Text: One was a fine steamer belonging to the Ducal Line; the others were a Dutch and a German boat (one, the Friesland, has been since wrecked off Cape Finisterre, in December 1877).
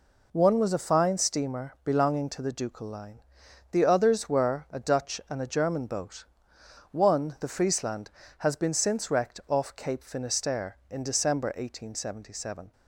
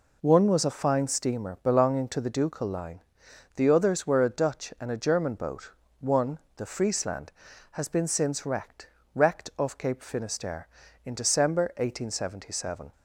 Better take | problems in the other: first | says "wrecked" twice; at 9.1 s

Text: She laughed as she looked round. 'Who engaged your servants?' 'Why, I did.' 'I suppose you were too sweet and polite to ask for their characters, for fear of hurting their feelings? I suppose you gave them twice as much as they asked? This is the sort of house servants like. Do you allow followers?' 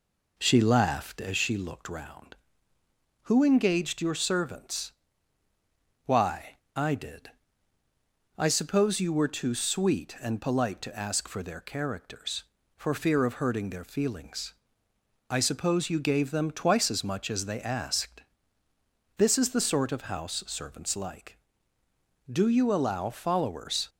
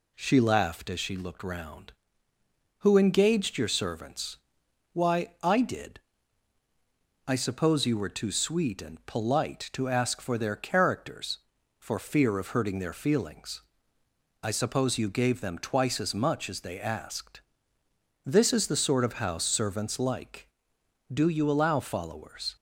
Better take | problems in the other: second | starts louder than the rest; until 1.3 s; 4 dB

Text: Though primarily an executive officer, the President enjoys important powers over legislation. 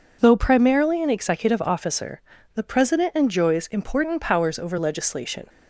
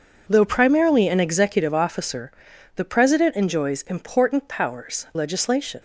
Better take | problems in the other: first | skips "over"; at 5.1 s

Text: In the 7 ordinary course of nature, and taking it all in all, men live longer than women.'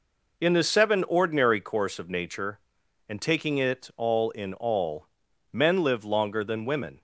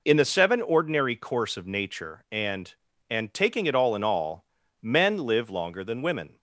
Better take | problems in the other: first | says "and" twice; at 3.0 s

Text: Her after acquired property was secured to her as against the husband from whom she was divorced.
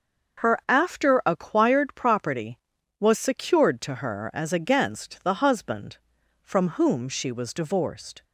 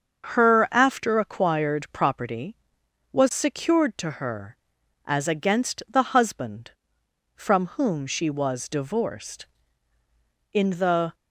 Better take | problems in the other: first | starts louder than the rest; until 1.3 s; 6.5 dB; noticeable in the first // goes on to say "In the"; noticeable; from 10.5 s on; 0.62 s long

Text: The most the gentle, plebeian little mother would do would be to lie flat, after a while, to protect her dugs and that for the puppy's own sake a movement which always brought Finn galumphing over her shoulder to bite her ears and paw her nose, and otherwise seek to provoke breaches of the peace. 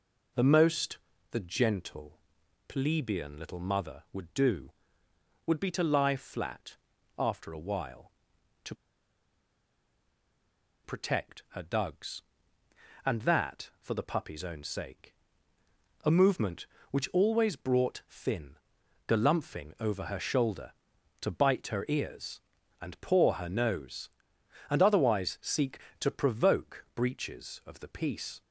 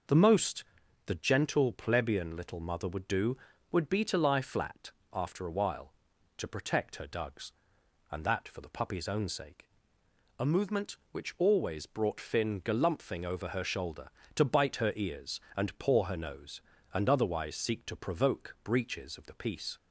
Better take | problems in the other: second | pauses between "most" and "the"; slight; at 0.9 s; 0.32 s long; also in the second // pauses between "to" and "protect"; strong; at 8.7 s; 2.1 s long // pauses between "sake" and "a"; noticeable; at 15.1 s; 0.92 s long; noticeable in the second // pauses between "Finn" and "galumphing"; noticeable; at 18.5 s; 0.52 s long

